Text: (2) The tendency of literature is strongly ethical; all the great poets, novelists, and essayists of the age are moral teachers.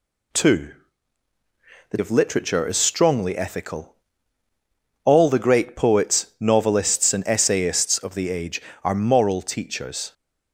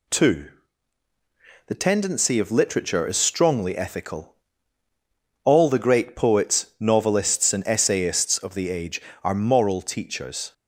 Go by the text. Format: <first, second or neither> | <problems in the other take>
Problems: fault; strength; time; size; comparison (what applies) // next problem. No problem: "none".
second | skips "tendency"; at 1.9 s